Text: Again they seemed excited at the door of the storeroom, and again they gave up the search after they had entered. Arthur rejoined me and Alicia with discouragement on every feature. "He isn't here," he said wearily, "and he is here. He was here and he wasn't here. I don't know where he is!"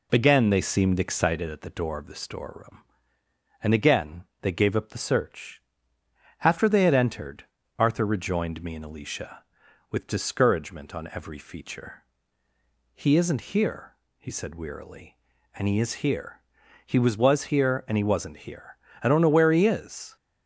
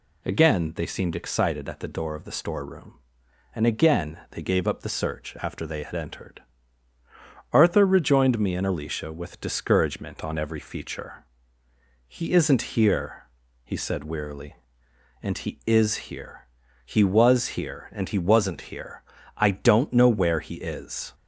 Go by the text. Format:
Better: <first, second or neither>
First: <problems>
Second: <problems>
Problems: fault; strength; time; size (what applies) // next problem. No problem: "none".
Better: second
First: pauses between "again" and "they"; slight; at 4.2 s; 0.18 s long // pauses between "search" and "after"; noticeable; at 5.6 s; 0.82 s long // says "was" twice; at 17.1 s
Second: none